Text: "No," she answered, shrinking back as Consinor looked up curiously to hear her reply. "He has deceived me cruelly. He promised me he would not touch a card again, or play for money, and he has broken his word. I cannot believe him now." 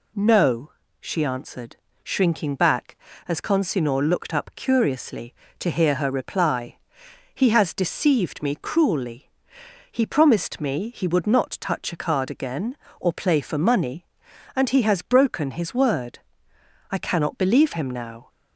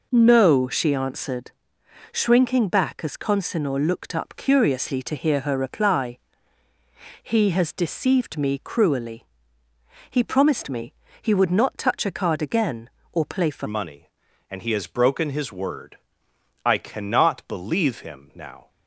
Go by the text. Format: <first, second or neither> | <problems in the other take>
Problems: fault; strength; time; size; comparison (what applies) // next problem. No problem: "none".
first | pauses between "me" and "he"; slight; at 10.9 s; 0.28 s long // changes voice at "money"; from 13.6 s on; 5.0 s long